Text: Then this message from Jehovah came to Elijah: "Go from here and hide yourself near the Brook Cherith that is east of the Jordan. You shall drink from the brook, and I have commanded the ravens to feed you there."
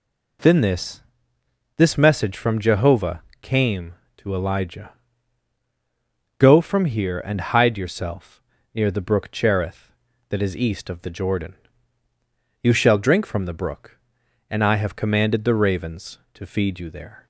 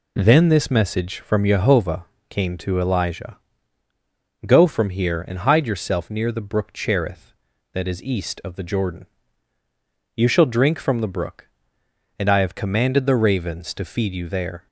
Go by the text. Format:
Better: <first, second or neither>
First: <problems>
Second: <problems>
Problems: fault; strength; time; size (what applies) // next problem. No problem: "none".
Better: second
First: says "this" twice; at 1.7 s // pauses between "Jehovah" and "came"; slight; at 3.2 s; 0.20 s long // pauses between "yourself" and "near"; slight; at 8.4 s; 0.32 s long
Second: pauses between "Jehovah" and "came"; slight; at 2.0 s; 0.24 s long